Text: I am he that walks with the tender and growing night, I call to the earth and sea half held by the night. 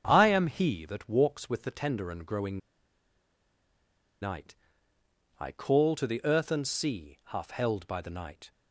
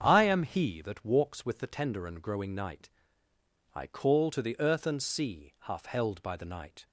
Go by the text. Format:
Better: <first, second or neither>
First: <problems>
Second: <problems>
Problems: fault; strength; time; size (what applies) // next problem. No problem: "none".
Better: second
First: starts louder than the rest; strong; until 1.0 s; 7.5 dB // pauses between "growing" and "night"; strong; at 2.5 s; 1.6 s long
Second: starts louder than the rest; strong; until 1.0 s; 7.5 dB